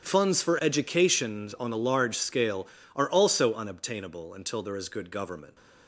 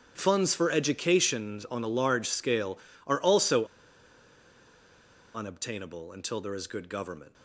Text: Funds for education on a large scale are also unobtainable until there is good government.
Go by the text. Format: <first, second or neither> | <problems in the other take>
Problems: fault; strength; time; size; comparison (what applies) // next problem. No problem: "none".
first | starts louder than the rest; strong; until 1.1 s; 8.5 dB; strong in the first // pauses between "also" and "unobtainable"; strong; at 3.6 s; 1.6 s long